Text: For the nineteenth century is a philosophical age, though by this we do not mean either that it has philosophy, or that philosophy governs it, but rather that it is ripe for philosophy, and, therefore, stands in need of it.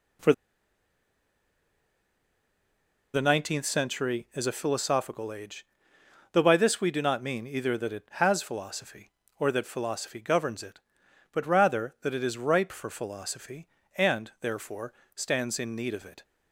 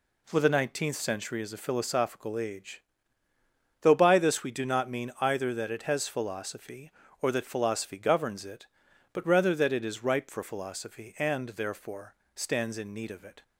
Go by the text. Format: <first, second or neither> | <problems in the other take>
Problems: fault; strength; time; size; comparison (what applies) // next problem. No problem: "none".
second | pauses between "For" and "the"; strong; at 0.3 s; 2.7 s long